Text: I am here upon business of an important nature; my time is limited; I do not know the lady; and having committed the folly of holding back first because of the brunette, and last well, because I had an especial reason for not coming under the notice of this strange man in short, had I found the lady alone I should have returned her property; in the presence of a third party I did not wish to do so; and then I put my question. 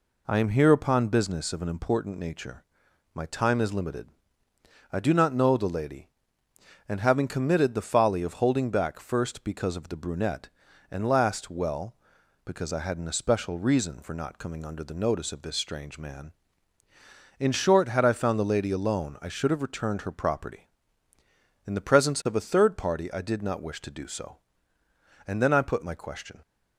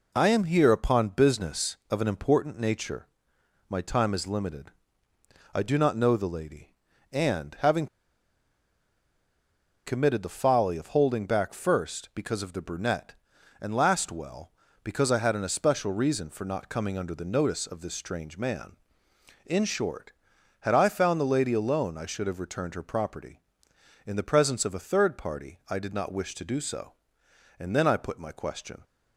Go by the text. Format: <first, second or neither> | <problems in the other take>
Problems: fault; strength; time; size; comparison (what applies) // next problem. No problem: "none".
first | pauses between "having" and "committed"; strong; at 7.8 s; 2.0 s long